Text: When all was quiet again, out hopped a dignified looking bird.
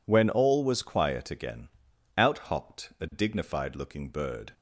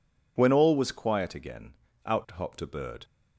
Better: first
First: none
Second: skips "dignified looking"; at 2.6 s

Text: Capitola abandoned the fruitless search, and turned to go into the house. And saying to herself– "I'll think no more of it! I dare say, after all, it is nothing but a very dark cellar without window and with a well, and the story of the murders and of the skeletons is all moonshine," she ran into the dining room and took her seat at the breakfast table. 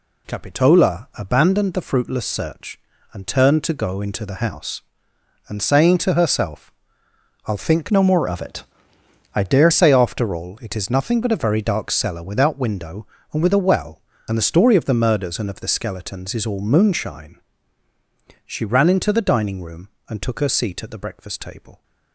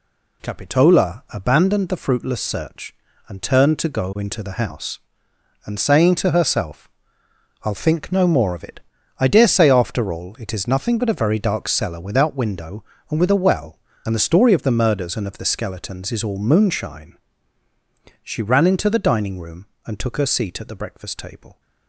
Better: second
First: changes voice from "no" to "dare"; from 7.9 to 9.7 s; 1.8 s long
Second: none

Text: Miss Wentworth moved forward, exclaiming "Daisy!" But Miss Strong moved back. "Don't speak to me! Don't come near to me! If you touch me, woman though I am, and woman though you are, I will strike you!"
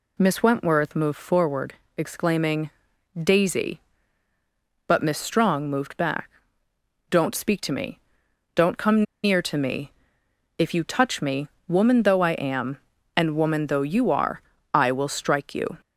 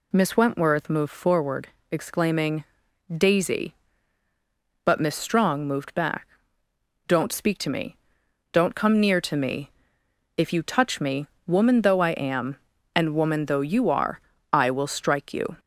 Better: second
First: pauses between "exclaiming" and "Daisy"; at 2.7 s; 0.44 s long // pauses between "come" and "near"; slight; at 9.0 s; 0.20 s long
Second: pauses between "exclaiming" and "Daisy"; at 2.6 s; 0.44 s long

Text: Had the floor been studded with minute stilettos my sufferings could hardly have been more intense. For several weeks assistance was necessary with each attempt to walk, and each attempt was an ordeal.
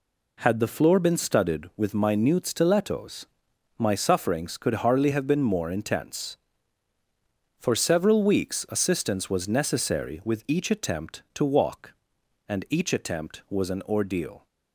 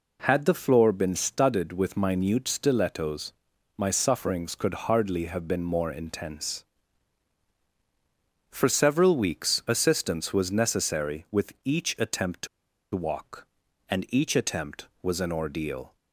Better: first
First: pauses between "stilettos" and "my"; noticeable; at 3.2 s; 0.50 s long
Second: pauses between "stilettos" and "my"; at 3.3 s; 0.42 s long // pauses between "to" and "walk"; noticeable; at 12.4 s; 0.47 s long

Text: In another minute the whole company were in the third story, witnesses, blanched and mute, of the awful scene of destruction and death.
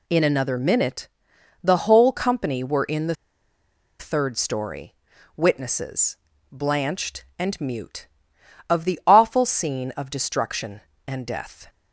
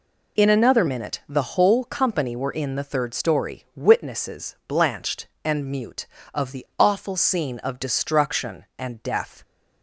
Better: second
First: pauses between "minute" and "the"; noticeable; at 1.0 s; 0.56 s long // pauses between "the" and "third"; noticeable; at 3.1 s; 0.84 s long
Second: none

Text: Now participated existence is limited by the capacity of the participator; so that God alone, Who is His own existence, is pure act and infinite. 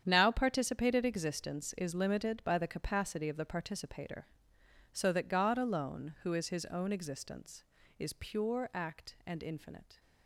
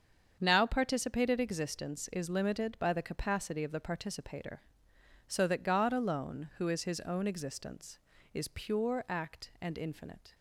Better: second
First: gets quieter; strong; throughout; 12.5 dB // starts louder than the rest; strong; until 1.0 s; 8.5 dB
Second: starts louder than the rest; strong; until 1.4 s; 7 dB

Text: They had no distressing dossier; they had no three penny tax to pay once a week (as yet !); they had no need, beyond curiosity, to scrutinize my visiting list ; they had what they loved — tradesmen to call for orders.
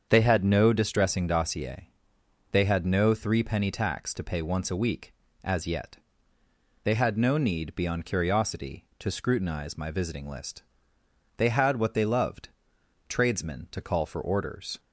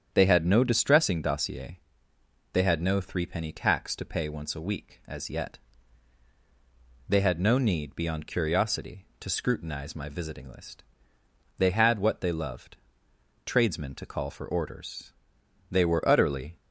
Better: first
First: starts louder than the rest; strong; until 1.1 s; 7.5 dB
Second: starts louder than the rest; strong; until 1.1 s; 8.5 dB // goes on to say "They were utterly"; noticeable; from 15.7 s on; 0.86 s long

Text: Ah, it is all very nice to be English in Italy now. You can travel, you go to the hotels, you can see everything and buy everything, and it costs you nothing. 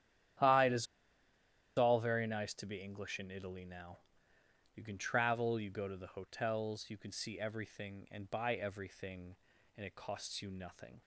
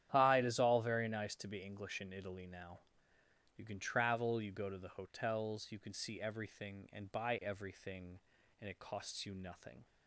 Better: second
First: starts louder than the rest; strong; until 2.3 s; 10.5 dB // pauses between "is" and "all"; noticeable; at 0.8 s; 0.91 s long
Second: starts louder than the rest; strong; until 1.1 s; 10.5 dB

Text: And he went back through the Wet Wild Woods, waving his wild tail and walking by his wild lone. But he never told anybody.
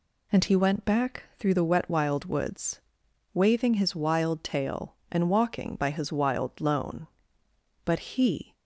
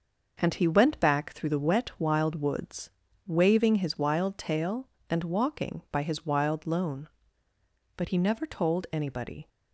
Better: second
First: pauses between "back" and "through"; slight; at 1.2 s; 0.16 s long // stops before "never told anybody"; at 8.5 s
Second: none

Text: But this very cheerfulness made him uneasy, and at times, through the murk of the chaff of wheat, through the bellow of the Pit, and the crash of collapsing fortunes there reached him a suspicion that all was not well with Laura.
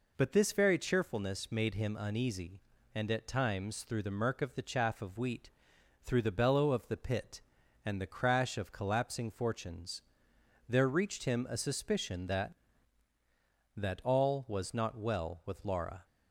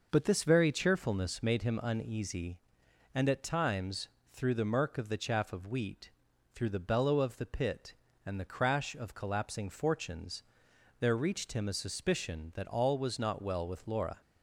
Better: second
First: pauses between "fortunes" and "there"; noticeable; at 10.0 s; 0.66 s long // says "that" twice; at 13.7 s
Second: pauses between "fortunes" and "there"; noticeable; at 10.4 s; 0.58 s long

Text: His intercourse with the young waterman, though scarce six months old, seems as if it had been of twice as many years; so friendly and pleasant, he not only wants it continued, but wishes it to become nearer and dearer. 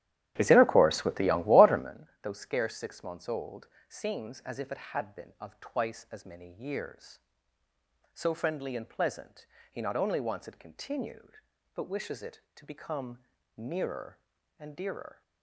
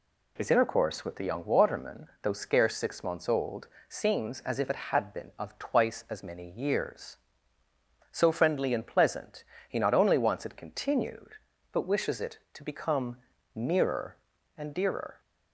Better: second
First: starts louder than the rest; strong; until 2.0 s; 12 dB // pauses between "become" and "nearer"; slight; at 13.1 s; 0.36 s long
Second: pauses between "become" and "nearer"; slight; at 13.1 s; 0.36 s long

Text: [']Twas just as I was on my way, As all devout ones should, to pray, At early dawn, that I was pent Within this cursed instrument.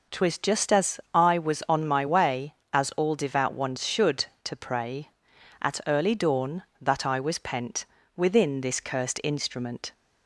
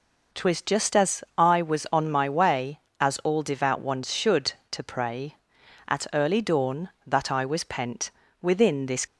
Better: first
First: pauses between "pent" and "Within"; slight; at 7.8 s; 0.28 s long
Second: pauses between "pent" and "Within"; slight; at 8.1 s; 0.28 s long // stops before "cursed instrument"; at 9.0 s

